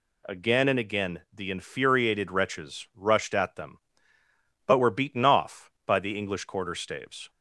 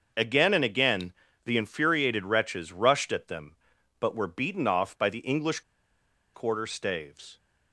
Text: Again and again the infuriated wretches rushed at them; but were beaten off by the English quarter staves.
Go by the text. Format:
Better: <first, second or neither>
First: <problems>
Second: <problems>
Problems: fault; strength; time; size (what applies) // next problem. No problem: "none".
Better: first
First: none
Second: starts louder than the rest; noticeable; until 1.4 s; 6 dB // pauses between "again" and "the"; slight; at 1.1 s; 0.32 s long // pauses between "English" and "quarter"; noticeable; at 5.6 s; 0.73 s long